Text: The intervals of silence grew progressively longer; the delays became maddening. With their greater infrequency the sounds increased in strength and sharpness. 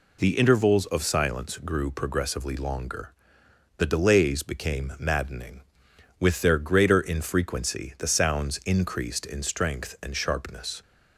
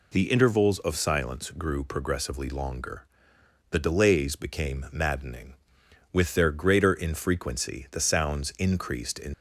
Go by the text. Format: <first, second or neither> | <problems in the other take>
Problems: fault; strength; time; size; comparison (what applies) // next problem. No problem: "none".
first | stops before "strength and sharpness"; at 9.3 s